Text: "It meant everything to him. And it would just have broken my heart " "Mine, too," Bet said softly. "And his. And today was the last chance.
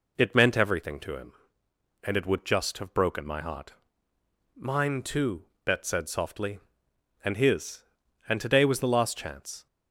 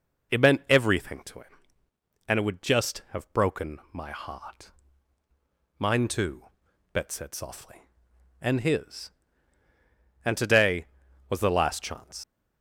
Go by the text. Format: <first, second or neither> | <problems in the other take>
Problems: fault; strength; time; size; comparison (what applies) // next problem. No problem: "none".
first | leaves "chance" unfinished; at 12.2 s; 80 ms